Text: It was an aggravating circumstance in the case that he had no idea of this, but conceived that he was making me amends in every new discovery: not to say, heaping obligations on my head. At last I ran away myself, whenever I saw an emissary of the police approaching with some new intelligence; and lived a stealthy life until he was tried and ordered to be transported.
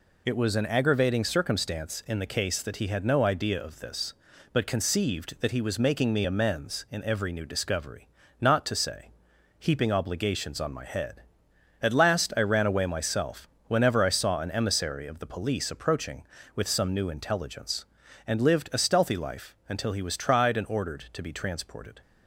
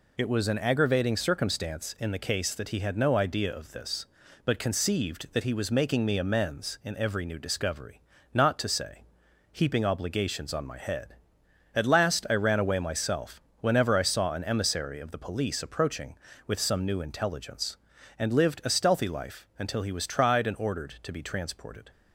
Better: neither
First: none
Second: none

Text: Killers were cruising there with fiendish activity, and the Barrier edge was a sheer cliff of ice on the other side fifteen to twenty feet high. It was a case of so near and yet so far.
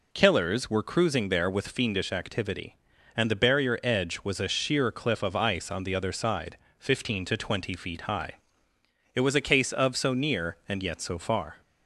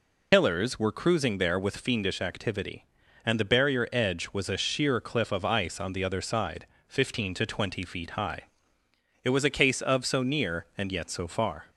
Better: first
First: pauses between "side" and "fifteen"; slight; at 6.5 s; 0.22 s long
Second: loses the start of "Killers"; at 0.3 s; 105 ms // pauses between "side" and "fifteen"; slight; at 6.6 s; 0.22 s long

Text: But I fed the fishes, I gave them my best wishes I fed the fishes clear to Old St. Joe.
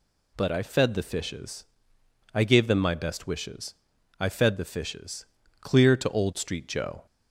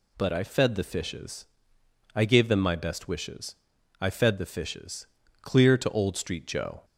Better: neither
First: pauses between "wishes" and "I"; at 3.7 s; 0.44 s long // pauses between "fishes" and "clear"; slight; at 5.2 s; 0.34 s long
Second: pauses between "wishes" and "I"; at 3.5 s; 0.44 s long // pauses between "fishes" and "clear"; slight; at 5.0 s; 0.34 s long

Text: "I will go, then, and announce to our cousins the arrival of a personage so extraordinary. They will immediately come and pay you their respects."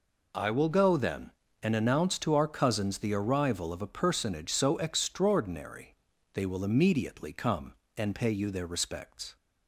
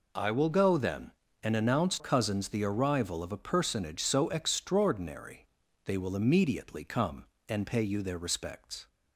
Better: first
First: none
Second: skips "to our"; at 1.9 s

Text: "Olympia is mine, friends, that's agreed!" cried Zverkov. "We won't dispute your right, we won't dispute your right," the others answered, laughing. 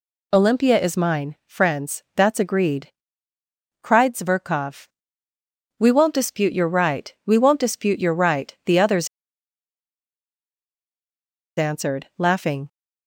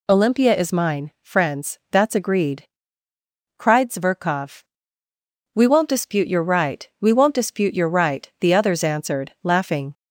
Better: second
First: pauses between "others" and "answered"; strong; at 9.0 s; 2.5 s long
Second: none

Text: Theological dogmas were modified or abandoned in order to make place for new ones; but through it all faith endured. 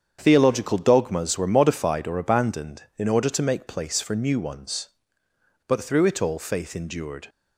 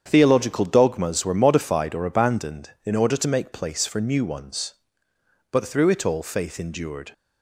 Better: neither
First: starts louder than the rest; strong; until 1.2 s; 7.5 dB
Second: starts louder than the rest; strong; until 1.0 s; 7.5 dB

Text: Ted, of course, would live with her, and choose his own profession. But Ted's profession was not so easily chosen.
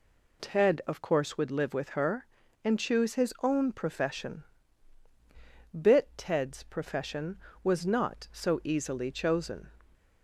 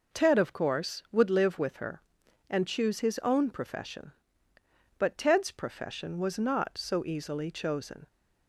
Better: second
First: says "Bit" for "But"; at 5.7 s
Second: none

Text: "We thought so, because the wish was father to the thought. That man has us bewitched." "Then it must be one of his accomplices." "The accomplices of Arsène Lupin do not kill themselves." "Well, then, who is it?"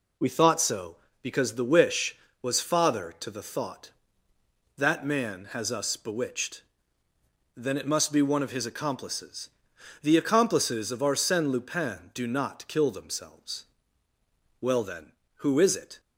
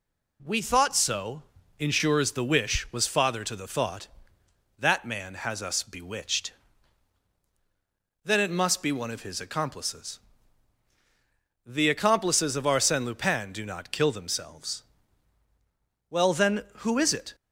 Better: first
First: none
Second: says "ensures" for "because"; at 1.7 s

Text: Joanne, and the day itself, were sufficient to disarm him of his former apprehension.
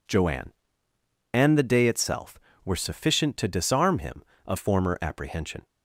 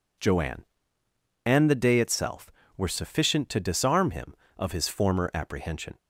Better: second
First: skips "his"; at 4.5 s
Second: none

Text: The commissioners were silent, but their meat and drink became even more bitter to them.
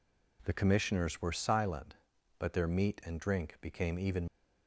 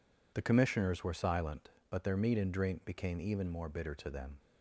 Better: second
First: stops before "more bitter to them"; at 4.2 s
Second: none

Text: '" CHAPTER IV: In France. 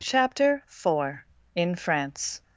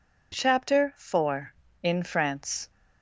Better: neither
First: none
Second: none

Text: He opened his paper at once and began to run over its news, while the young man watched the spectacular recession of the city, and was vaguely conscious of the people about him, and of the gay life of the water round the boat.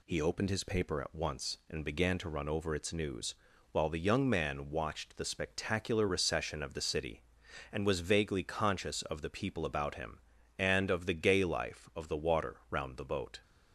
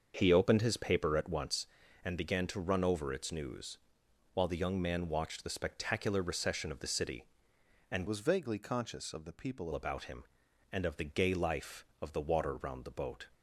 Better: first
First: none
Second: starts louder than the rest; until 1.1 s; 6.5 dB // changes voice from "was" to "people"; from 8.0 to 9.6 s; 1.6 s long

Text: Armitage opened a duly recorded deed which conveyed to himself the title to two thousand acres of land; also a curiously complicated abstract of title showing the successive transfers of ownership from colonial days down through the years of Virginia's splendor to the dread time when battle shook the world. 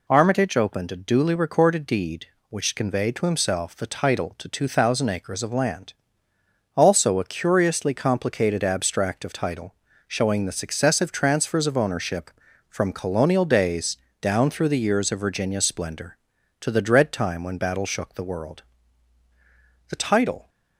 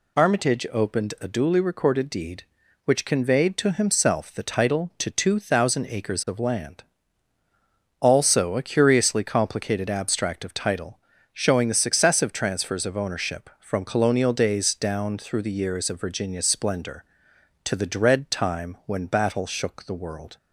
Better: second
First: pauses between "title" and "showing"; slight; at 9.7 s; 0.34 s long // pauses between "days" and "down"; slight; at 13.9 s; 0.24 s long // goes on to say "The title"; from 19.8 s on; 0.60 s long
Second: pauses between "title" and "showing"; slight; at 10.9 s; 0.34 s long

